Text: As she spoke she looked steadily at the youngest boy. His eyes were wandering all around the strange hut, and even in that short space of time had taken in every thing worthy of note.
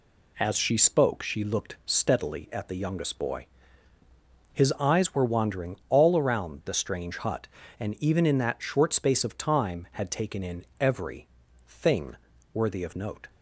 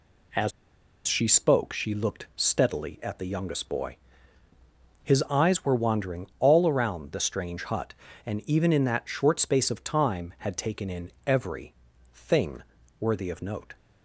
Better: first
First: pauses between "every" and "thing"; at 11.2 s; 0.38 s long // pauses between "thing" and "worthy"; at 12.1 s; 0.38 s long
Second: pauses between "As" and "she"; noticeable; at 0.5 s; 0.56 s long // pauses between "every" and "thing"; at 11.7 s; 0.38 s long // pauses between "thing" and "worthy"; at 12.6 s; 0.38 s long

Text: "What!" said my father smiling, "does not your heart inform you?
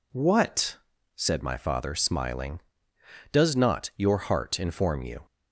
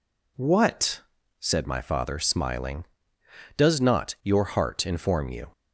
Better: neither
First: none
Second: none

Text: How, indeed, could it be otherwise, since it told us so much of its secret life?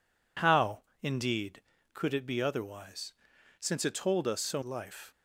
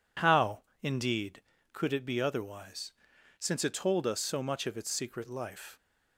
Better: second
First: skips "much of its secret"; at 4.6 s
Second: none

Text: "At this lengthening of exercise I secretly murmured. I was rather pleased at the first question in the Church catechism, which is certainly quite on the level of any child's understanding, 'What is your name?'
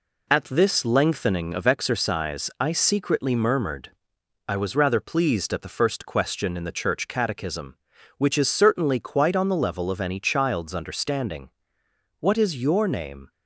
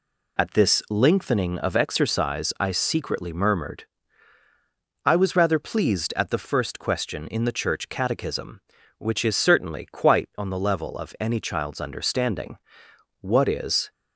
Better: first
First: none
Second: stops before "your name"; at 13.9 s

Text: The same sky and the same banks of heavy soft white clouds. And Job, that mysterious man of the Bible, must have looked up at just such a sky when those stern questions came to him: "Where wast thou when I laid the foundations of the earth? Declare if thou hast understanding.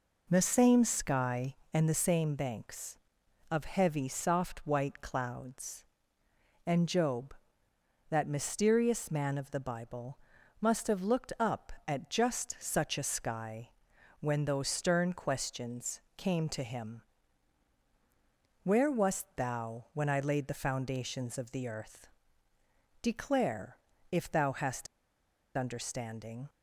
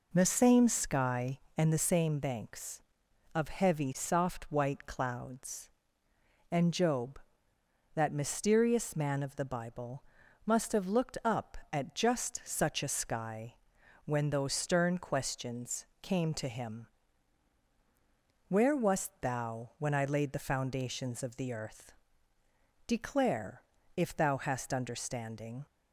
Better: second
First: pauses between "sky" and "when"; noticeable; at 13.7 s; 0.50 s long // pauses between "questions" and "came"; slight; at 16.0 s; 0.16 s long // pauses between "Declare" and "if"; slight; at 23.7 s; 0.32 s long // pauses between "hast" and "understanding"; noticeable; at 24.8 s; 0.72 s long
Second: pauses between "sky" and "when"; noticeable; at 13.5 s; 0.50 s long // pauses between "questions" and "came"; slight; at 15.8 s; 0.16 s long // pauses between "Declare" and "if"; slight; at 23.6 s; 0.32 s long

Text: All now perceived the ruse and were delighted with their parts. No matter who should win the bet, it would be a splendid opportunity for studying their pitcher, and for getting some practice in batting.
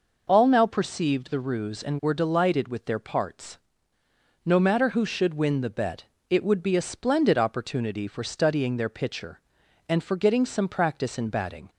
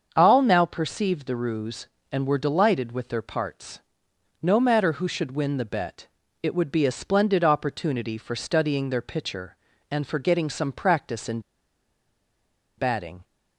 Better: first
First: none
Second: starts louder than the rest; until 1.1 s; 7 dB // pauses between "in" and "batting"; strong; at 11.4 s; 1.3 s long

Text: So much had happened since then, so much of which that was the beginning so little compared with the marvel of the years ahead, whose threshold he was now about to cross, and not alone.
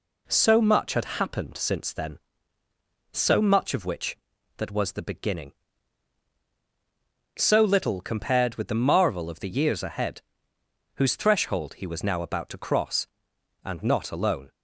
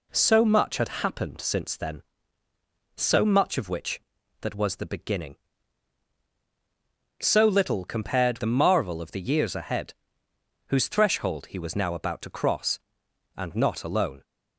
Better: first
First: none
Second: skips "with"; at 8.3 s

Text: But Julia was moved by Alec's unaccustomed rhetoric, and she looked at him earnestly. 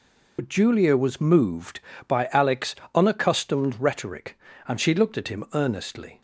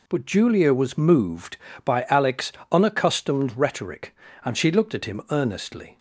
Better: second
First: loses the start of "But"; at 0.3 s; 80 ms // pauses between "Alec's" and "unaccustomed"; slight; at 2.7 s; 0.18 s long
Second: pauses between "Alec's" and "unaccustomed"; slight; at 2.5 s; 0.18 s long

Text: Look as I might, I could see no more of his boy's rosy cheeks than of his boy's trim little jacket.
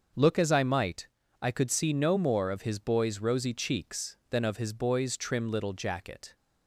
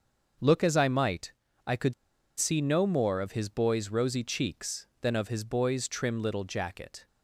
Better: first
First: starts louder than the rest; until 1.4 s; 6.5 dB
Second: starts louder than the rest; until 1.7 s; 6.5 dB // pauses between "could" and "see"; noticeable; at 1.9 s; 0.46 s long

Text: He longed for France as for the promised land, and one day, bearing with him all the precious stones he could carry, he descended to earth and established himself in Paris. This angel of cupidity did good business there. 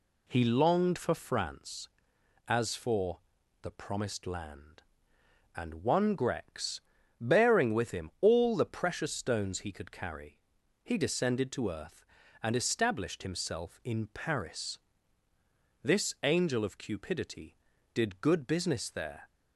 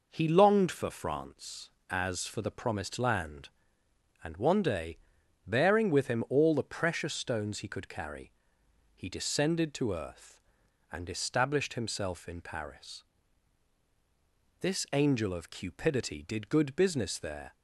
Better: second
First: pauses between "for" and "the"; at 3.1 s; 0.42 s long // says "grex" for "day"; at 6.1 s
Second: none

